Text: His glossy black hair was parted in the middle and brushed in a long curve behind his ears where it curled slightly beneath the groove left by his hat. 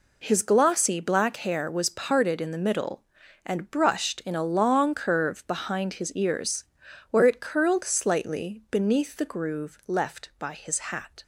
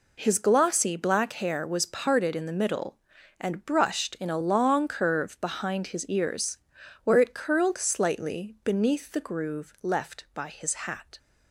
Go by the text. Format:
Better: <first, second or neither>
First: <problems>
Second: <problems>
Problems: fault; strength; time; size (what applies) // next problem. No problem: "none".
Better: neither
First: pauses between "ears" and "where"; noticeable; at 6.6 s; 0.48 s long // pauses between "his" and "hat"; slight; at 10.7 s; 0.16 s long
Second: pauses between "ears" and "where"; noticeable; at 6.5 s; 0.48 s long // pauses between "his" and "hat"; slight; at 10.7 s; 0.16 s long